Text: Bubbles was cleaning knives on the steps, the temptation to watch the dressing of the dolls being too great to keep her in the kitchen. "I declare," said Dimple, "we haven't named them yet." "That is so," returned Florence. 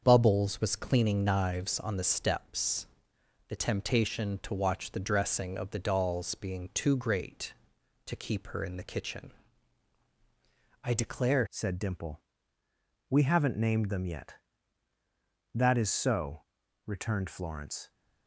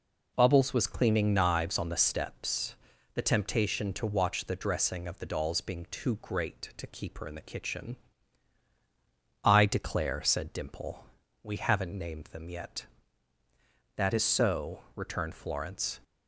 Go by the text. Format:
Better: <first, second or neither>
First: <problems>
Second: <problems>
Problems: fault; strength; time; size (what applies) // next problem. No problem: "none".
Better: second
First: starts louder than the rest; until 1.0 s; 6.5 dB // changes voice at "said"; from 11.4 s on; 6.4 s long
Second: none